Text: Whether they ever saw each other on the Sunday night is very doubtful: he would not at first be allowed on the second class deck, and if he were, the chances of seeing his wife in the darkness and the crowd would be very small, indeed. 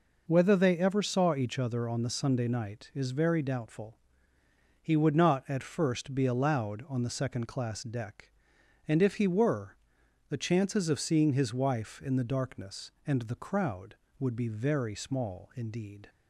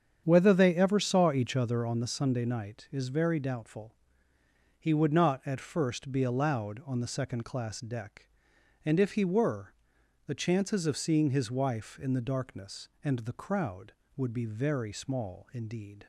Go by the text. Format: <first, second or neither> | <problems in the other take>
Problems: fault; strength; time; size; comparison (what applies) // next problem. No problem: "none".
first | starts louder than the rest; strong; until 2.1 s; 8 dB